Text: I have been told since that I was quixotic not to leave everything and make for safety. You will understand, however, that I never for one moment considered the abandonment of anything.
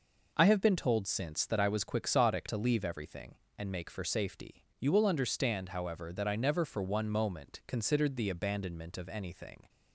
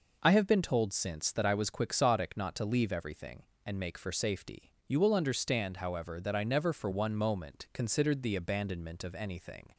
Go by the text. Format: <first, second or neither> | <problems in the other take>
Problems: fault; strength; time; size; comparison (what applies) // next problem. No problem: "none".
second | skips "not"; at 2.4 s